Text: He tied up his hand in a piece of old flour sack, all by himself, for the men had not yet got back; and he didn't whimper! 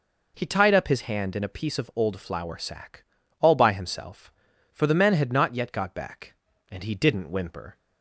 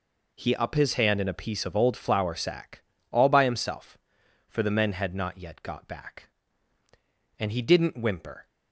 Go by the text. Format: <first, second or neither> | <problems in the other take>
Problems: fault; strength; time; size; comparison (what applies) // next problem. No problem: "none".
first | skips "tied"; at 0.5 s